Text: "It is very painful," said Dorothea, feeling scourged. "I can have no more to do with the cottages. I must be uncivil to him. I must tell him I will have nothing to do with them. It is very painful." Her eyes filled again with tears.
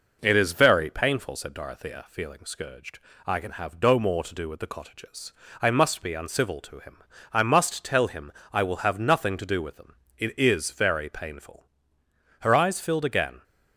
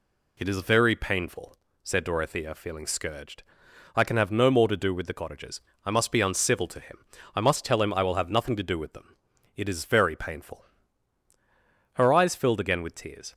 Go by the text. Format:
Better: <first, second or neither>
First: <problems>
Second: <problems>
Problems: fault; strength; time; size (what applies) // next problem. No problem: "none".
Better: second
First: pauses between "him" and "I"; slight; at 8.3 s; 0.18 s long // stops before "with tears"; at 13.4 s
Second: none